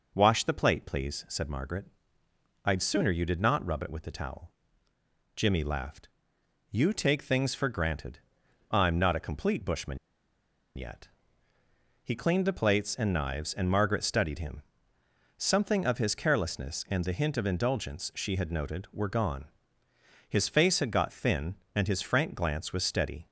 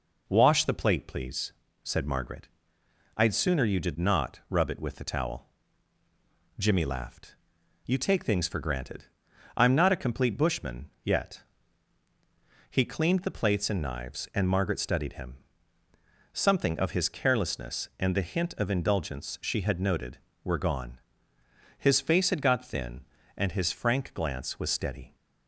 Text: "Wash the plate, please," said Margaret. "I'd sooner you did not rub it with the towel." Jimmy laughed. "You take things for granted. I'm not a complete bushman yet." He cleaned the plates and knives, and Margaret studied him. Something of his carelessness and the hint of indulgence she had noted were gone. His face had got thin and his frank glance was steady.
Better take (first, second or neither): second